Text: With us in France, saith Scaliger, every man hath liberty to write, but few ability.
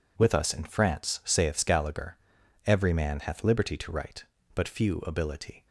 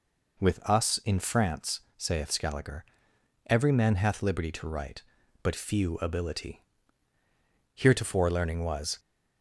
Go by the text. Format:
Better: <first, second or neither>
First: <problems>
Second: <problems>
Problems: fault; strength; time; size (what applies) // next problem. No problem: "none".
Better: first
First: none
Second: goes on to say "Heretofore learning was"; noticeable; from 7.7 s on; 1.2 s long